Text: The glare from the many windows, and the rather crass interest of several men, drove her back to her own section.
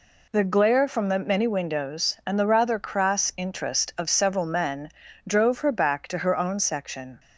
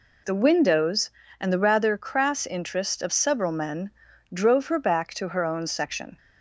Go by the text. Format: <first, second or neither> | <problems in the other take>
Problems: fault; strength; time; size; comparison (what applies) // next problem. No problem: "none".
first | skips "glare from the many"; at 0.4 s